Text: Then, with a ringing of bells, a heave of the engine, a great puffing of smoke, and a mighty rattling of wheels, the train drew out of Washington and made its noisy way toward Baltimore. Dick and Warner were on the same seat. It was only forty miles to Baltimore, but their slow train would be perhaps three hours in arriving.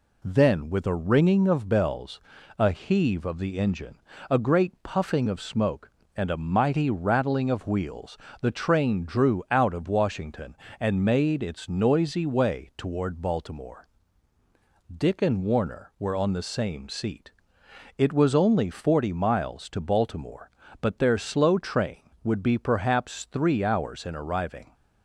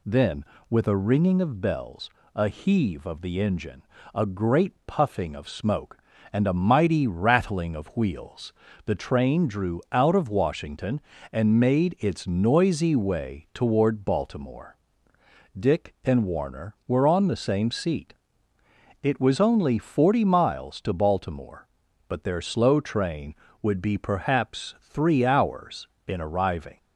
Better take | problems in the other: neither | none

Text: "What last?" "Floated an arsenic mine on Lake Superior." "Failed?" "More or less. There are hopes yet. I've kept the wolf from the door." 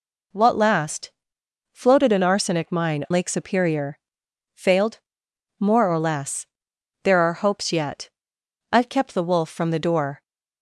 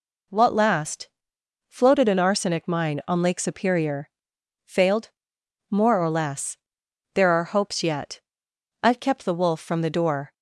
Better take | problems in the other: second | skips "on"; at 3.0 s

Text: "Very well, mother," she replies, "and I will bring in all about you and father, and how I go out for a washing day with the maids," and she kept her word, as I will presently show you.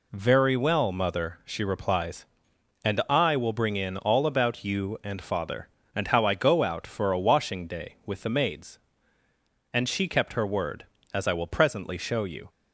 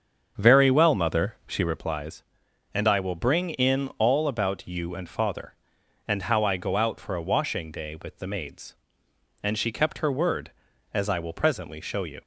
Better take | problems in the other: first | starts louder than the rest; until 1.9 s; 7 dB

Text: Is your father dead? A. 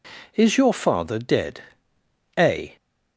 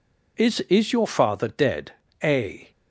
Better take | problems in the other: first | says "Is" twice; at 0.6 s

